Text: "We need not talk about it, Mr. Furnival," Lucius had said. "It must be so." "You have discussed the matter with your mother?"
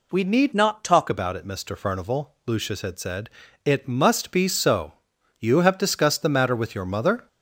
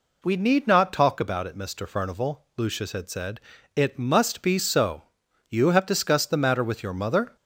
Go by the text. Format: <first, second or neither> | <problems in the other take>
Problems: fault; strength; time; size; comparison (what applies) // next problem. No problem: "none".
second | changes voice from "not" to "talk"; from 0.5 to 1.0 s; 0.5 s long